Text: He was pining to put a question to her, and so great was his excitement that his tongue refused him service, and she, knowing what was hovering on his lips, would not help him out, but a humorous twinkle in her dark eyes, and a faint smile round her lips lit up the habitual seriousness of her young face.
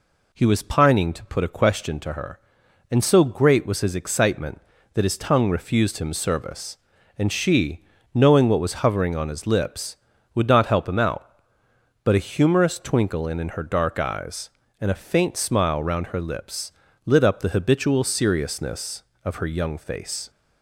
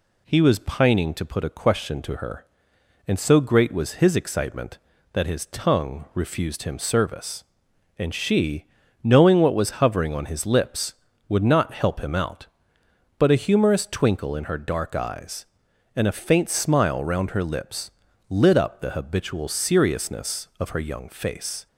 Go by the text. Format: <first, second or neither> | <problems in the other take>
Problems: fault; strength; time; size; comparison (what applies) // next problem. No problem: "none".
second | says "in" twice; at 13.3 s // pauses between "lips" and "lit"; slight; at 16.7 s; 0.32 s long; slight in the second